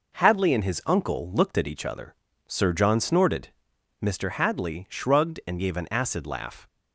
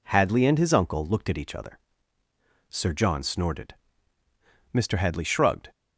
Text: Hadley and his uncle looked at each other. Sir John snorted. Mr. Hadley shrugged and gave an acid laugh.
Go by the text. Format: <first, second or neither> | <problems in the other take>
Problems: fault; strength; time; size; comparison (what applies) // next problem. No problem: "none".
first | stops before "and gave an acid laugh"; at 5.7 s